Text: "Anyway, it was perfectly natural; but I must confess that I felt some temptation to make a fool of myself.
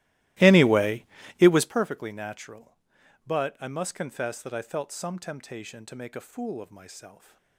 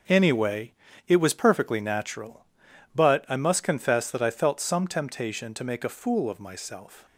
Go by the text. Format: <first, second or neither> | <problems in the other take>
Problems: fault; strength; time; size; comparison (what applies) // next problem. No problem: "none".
second | starts louder than the rest; strong; until 1.8 s; 17.5 dB